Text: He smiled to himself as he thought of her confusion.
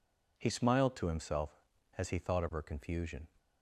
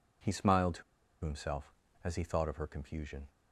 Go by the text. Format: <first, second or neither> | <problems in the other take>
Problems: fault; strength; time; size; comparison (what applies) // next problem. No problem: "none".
first | pauses between "to" and "himself"; at 0.8 s; 0.41 s long